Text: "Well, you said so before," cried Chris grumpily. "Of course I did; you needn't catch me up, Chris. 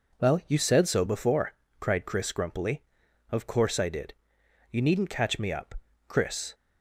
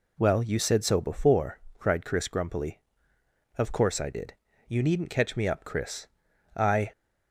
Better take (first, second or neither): first